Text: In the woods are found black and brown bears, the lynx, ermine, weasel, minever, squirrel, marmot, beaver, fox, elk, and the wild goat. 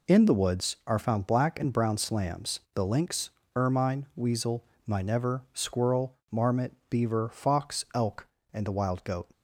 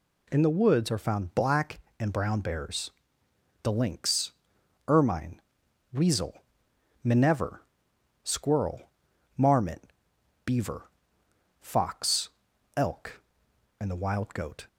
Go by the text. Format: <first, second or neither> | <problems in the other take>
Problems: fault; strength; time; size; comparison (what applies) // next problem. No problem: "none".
second | says "slams" for "bears"; at 1.9 s